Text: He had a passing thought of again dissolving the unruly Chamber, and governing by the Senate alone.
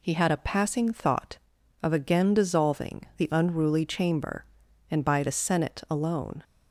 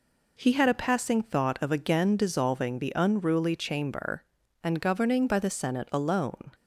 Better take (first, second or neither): second